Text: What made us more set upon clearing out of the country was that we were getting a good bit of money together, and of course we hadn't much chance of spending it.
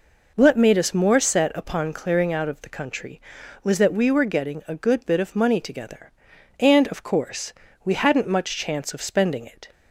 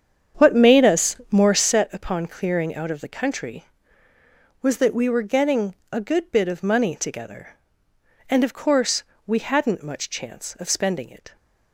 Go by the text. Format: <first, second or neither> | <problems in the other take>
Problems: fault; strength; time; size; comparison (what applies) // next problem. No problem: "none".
first | starts louder than the rest; strong; until 1.8 s; 8 dB // pauses between "us" and "more"; slight; at 1.1 s; 0.16 s long // pauses between "getting" and "a"; slight; at 5.7 s; 0.20 s long // pauses between "course" and "we"; slight; at 9.0 s; 0.22 s long; slight in the first